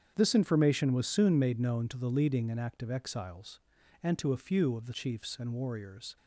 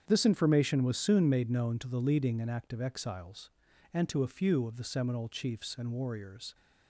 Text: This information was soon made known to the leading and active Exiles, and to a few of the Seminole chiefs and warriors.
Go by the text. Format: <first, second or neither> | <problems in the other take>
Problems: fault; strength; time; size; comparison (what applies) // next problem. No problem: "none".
second | starts louder than the rest; strong; until 1.1 s; 8 dB; strong in the second // skips "Seminole"; at 4.9 s